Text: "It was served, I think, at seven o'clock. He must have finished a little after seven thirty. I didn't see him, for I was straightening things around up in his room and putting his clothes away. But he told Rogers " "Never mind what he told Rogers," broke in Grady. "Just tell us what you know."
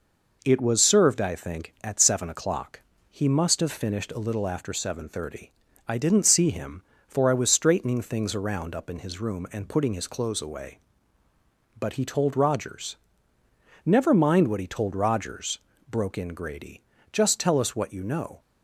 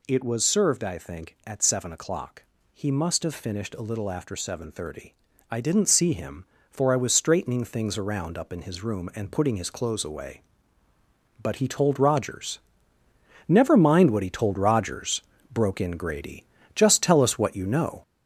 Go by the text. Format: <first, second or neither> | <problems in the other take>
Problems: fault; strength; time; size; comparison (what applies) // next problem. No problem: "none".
first | gets louder; noticeable; throughout; 4 dB